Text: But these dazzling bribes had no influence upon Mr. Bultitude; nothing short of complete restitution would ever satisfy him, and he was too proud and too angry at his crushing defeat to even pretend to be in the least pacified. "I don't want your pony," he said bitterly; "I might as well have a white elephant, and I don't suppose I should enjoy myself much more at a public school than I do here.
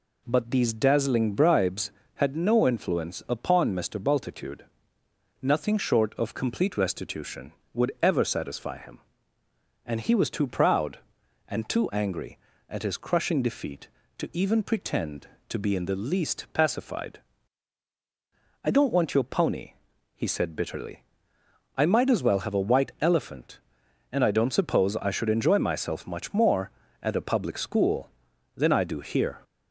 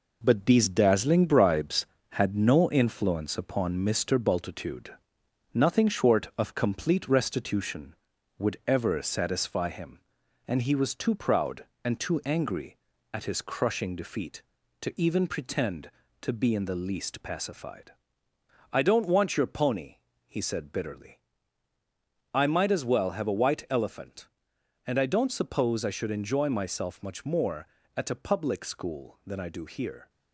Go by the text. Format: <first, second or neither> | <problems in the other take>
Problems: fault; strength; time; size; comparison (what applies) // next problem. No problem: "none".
first | gets quieter; noticeable; throughout; 5.5 dB